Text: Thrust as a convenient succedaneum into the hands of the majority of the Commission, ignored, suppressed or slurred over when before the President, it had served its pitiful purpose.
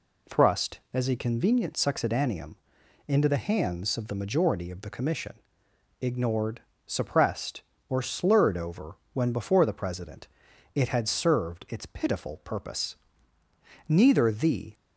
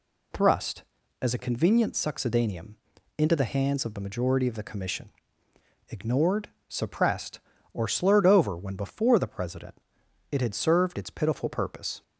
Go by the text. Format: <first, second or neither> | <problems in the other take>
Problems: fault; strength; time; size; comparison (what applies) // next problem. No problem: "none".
second | pauses between "succedaneum" and "into"; noticeable; at 2.5 s; 0.52 s long; also in the second // pauses between "over" and "when"; slight; at 8.9 s; 0.18 s long // goes on to say "Neither the"; noticeable; from 13.8 s on; 0.86 s long